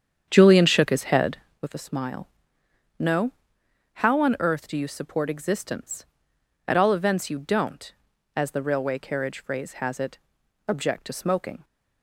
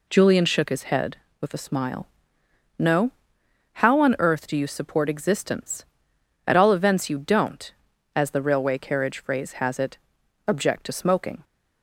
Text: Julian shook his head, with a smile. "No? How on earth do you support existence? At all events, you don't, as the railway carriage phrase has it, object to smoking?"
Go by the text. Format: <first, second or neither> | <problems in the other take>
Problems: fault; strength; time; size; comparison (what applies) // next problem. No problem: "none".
second | starts louder than the rest; strong; until 1.7 s; 8 dB